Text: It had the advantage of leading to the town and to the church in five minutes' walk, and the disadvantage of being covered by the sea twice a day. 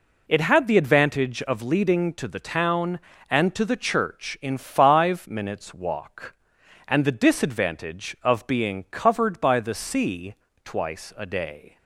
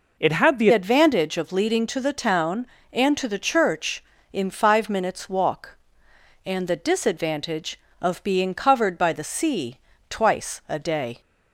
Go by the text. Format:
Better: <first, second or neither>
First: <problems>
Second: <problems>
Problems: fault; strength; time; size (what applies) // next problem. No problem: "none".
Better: first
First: pauses between "sea" and "twice"; slight; at 10.3 s; 0.28 s long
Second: changes voice at "advantage"; from 0.7 s on; 10.5 s long // pauses between "sea" and "twice"; slight; at 9.7 s; 0.32 s long